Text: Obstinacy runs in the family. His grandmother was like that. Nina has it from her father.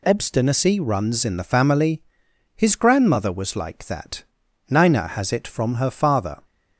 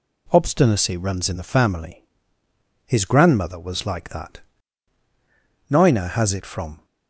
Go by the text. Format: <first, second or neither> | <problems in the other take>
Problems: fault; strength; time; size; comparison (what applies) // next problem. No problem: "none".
first | stops before "her father"; at 6.8 s